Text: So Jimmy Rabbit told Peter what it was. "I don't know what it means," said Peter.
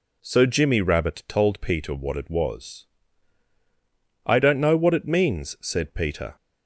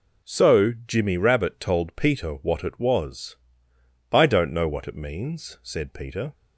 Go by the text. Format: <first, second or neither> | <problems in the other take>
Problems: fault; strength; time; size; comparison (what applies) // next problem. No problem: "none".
neither | none